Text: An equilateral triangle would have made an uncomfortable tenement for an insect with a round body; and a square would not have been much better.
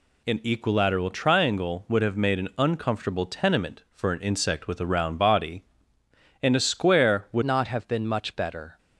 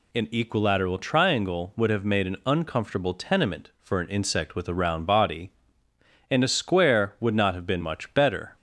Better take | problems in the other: second | changes voice at "not"; from 7.4 s on; 1.3 s long

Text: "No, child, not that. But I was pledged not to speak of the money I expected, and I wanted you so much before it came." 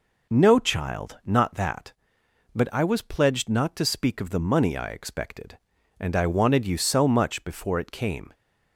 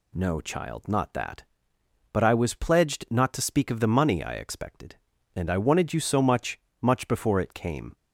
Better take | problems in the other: first | says "much" twice; at 6.8 s

